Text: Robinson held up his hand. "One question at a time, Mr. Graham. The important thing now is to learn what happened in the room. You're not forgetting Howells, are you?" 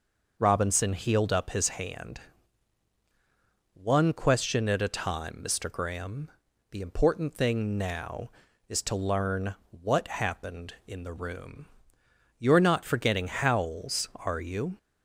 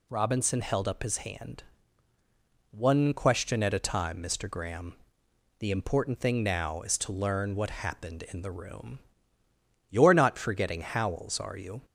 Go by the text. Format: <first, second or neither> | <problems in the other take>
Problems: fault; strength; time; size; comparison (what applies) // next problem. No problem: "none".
second | says "healed" for "held"; at 0.9 s // pauses between "learn" and "what"; slight; at 9.5 s; 0.16 s long